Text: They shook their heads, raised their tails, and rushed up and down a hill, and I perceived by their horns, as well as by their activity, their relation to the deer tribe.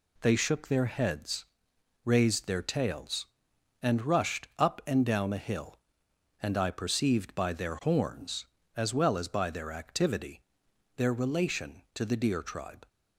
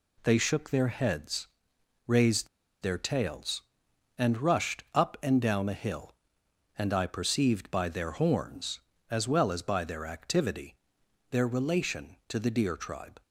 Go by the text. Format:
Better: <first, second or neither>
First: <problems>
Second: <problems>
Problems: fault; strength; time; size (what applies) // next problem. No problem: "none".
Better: first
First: none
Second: pauses between "raised" and "their"; slight; at 2.4 s; 0.34 s long